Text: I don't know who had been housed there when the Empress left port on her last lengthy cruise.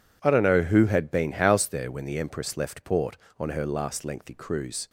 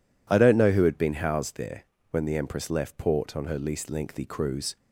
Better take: first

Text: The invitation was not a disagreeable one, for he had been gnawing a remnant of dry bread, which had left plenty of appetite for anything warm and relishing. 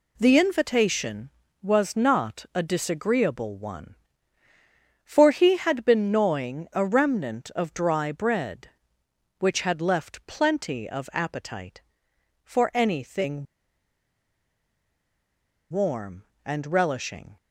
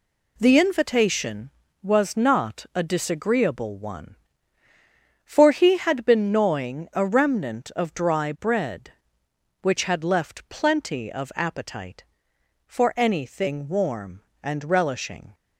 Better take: second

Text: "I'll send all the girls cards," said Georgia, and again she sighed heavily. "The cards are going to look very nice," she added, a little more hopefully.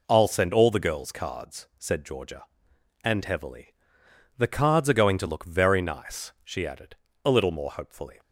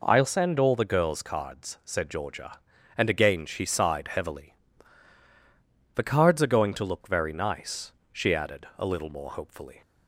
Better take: second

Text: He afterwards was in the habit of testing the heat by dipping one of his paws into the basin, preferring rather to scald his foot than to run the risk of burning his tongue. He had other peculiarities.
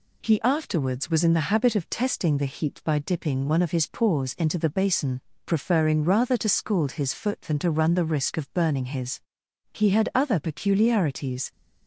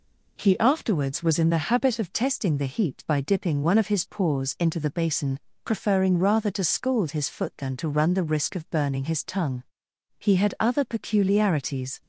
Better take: second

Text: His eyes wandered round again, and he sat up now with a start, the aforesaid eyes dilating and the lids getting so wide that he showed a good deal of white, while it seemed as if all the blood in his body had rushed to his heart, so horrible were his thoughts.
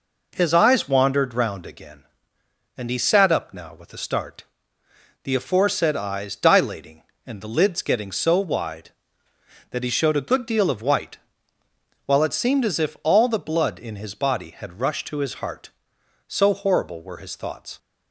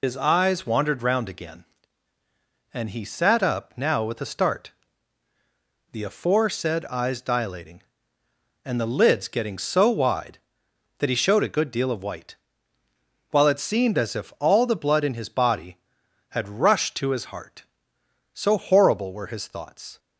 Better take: first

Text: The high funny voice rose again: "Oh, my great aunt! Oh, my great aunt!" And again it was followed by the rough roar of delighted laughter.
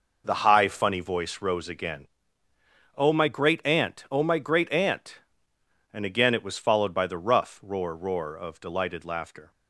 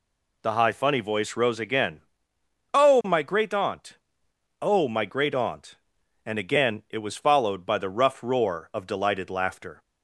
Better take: second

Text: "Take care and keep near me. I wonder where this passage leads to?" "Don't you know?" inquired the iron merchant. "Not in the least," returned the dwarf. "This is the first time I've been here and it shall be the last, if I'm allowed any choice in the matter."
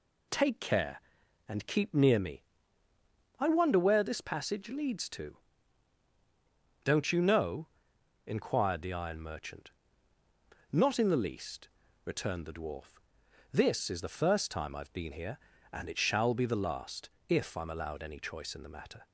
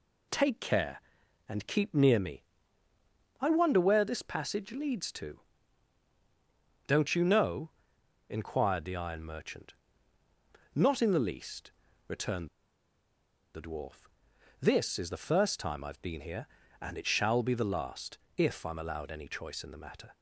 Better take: first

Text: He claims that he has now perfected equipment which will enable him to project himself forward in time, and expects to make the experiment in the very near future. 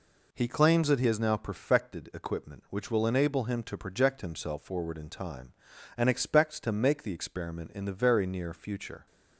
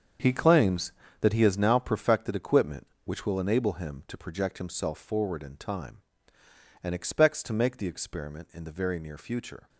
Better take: first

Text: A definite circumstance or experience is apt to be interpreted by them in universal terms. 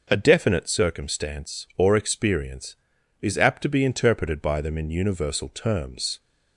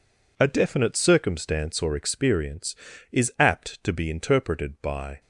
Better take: first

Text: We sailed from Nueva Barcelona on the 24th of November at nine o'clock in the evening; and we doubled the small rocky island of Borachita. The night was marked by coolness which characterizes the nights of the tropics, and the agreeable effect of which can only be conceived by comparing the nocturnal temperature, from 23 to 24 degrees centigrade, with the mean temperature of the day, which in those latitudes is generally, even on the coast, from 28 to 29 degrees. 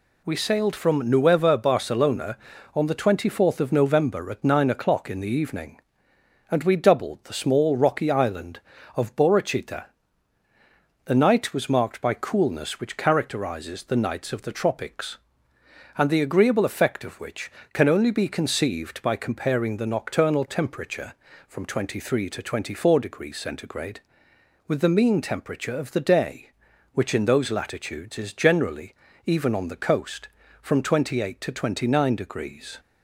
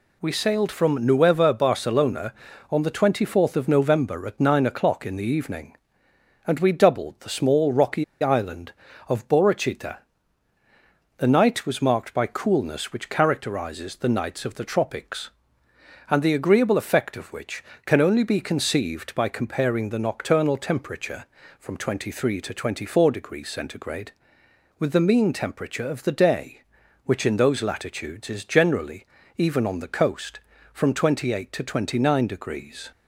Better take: first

